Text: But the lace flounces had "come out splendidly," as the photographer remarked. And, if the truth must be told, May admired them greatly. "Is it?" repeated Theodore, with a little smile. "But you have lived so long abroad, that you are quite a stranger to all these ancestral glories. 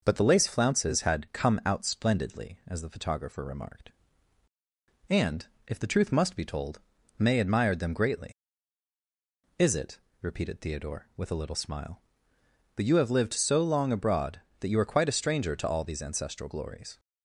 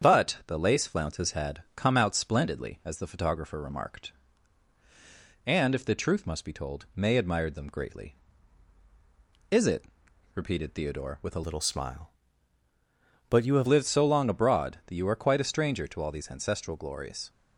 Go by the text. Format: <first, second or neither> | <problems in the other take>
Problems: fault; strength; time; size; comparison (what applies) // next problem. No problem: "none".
first | starts louder than the rest; strong; until 1.1 s; 8 dB // changes voice from "little" to "have"; from 11.4 to 13.6 s; 2.2 s long